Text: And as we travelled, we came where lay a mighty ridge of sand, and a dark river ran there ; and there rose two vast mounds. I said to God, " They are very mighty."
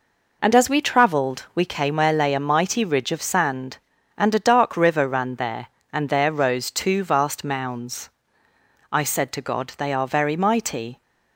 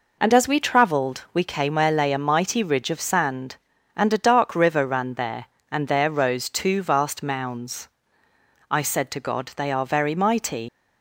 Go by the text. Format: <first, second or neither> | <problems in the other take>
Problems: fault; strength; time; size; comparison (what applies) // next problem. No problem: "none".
first | leaves "mighty" unfinished; at 10.6 s; 115 ms